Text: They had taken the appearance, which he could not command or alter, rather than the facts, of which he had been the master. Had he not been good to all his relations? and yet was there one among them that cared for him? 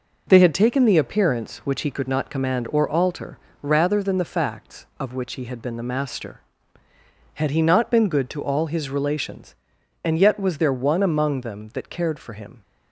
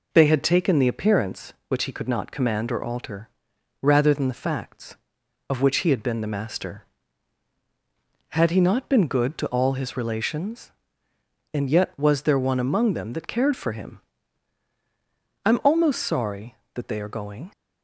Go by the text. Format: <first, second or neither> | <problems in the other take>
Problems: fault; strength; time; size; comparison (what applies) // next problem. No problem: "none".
first | goes on to say "I'm almost sorry that they are going"; strong; from 15.4 s on; 2.0 s long